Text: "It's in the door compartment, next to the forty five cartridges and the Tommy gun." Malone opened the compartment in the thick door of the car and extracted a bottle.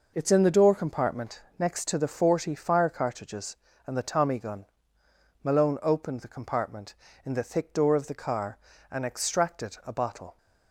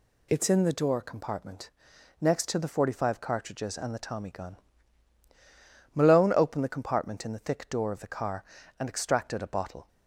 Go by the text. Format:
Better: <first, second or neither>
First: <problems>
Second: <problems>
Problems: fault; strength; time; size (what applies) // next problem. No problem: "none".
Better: second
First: says "fire" for "five"; at 2.5 s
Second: none